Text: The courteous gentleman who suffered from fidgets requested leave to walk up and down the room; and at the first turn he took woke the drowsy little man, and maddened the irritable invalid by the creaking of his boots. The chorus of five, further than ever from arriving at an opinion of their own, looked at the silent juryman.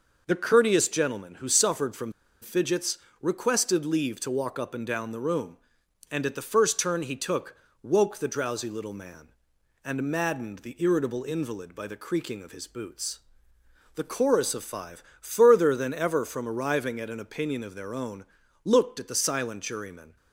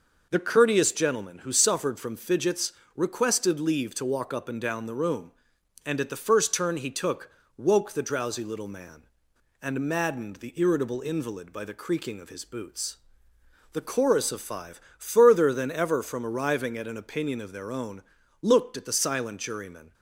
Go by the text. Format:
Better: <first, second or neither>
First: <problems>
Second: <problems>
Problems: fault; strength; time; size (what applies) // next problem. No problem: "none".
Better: second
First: pauses between "from" and "fidgets"; slight; at 2.1 s; 0.29 s long // pauses between "fidgets" and "requested"; slight; at 2.9 s; 0.24 s long // pauses between "took" and "woke"; slight; at 7.5 s; 0.26 s long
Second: pauses between "fidgets" and "requested"; slight; at 2.7 s; 0.24 s long // pauses between "took" and "woke"; slight; at 7.3 s; 0.26 s long